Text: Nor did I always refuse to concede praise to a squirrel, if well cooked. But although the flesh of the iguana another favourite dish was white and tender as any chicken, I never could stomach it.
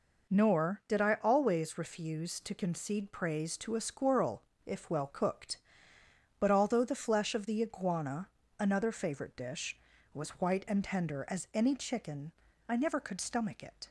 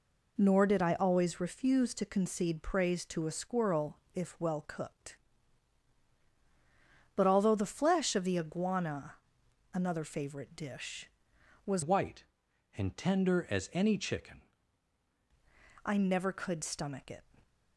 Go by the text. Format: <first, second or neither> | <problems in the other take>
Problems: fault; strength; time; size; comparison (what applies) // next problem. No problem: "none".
first | pauses between "iguana" and "another"; noticeable; at 9.1 s; 0.60 s long; slight in the first // changes voice from "white" to "chicken"; from 11.8 to 14.4 s; 2.6 s long